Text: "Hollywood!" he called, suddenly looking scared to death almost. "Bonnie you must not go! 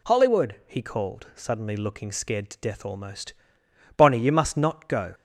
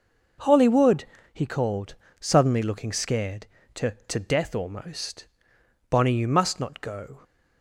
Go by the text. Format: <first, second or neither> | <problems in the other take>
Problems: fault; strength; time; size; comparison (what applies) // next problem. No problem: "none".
first | says "to" twice; at 4.0 s